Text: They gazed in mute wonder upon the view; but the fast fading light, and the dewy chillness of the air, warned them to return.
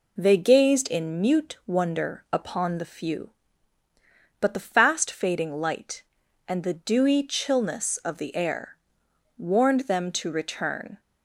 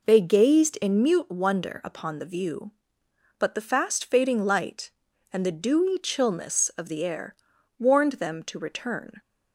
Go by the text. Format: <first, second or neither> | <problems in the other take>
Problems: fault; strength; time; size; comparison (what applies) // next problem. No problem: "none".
second | says "few" for "view"; at 2.8 s